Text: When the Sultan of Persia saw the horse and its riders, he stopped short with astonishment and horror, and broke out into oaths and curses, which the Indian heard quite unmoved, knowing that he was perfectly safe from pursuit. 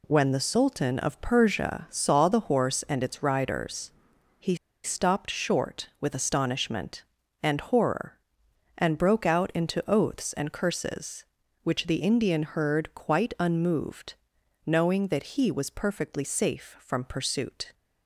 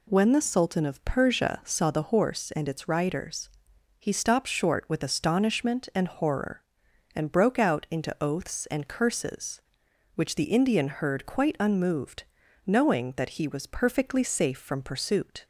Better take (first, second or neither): second